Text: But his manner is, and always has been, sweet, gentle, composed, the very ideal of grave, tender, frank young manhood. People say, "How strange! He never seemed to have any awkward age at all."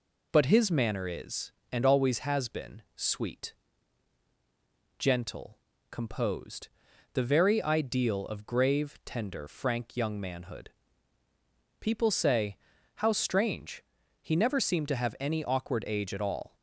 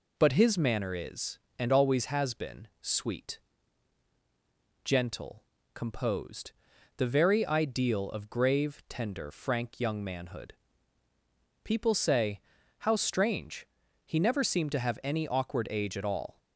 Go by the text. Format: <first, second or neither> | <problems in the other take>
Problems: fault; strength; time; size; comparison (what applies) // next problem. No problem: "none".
neither | none